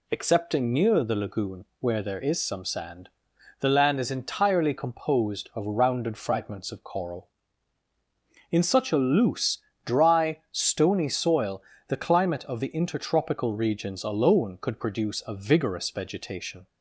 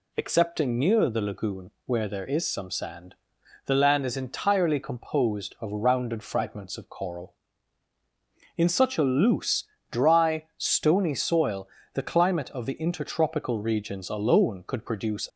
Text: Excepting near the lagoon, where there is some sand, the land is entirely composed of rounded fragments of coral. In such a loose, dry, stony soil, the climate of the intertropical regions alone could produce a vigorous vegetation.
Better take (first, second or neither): first